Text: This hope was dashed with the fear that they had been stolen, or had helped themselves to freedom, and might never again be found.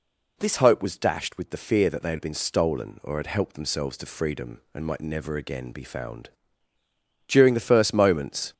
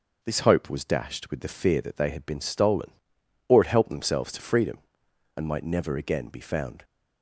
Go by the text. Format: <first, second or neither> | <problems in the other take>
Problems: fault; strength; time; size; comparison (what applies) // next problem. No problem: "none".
second | goes on to say "During the first moments"; noticeable; from 7.2 s on; 1.2 s long